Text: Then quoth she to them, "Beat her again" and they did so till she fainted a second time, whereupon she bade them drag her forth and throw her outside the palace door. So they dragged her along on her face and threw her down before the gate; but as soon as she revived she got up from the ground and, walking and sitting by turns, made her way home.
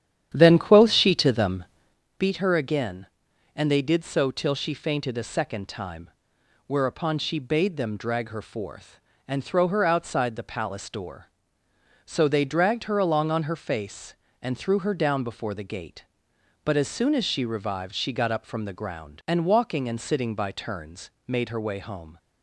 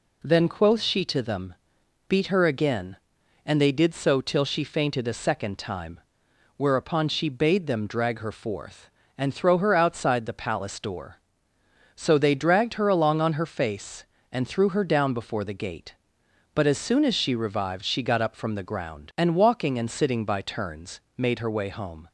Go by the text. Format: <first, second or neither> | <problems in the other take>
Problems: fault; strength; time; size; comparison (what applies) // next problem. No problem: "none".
second | starts louder than the rest; strong; until 2.0 s; 10 dB